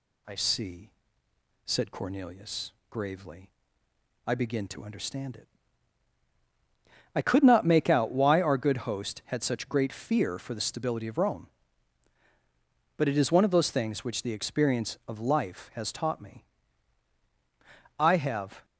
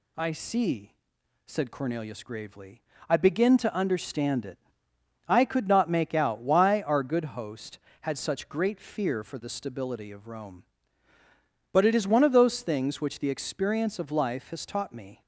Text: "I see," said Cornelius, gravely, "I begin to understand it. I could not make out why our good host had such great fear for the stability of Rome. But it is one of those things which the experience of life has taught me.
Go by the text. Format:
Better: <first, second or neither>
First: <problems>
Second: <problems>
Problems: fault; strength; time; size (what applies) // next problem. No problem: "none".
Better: second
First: goes on to say "I have"; noticeable; from 17.9 s on; 0.66 s long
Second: none